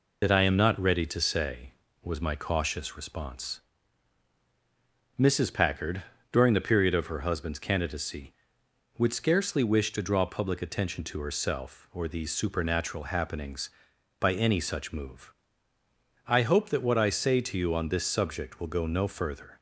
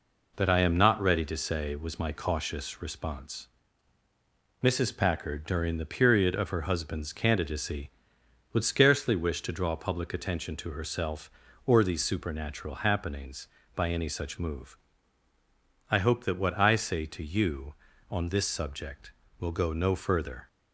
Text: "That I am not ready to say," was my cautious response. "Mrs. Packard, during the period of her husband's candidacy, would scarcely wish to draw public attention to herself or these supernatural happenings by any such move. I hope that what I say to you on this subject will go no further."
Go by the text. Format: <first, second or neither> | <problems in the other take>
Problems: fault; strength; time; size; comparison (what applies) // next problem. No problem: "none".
second | loses the start of "That"; at 0.2 s; 50 ms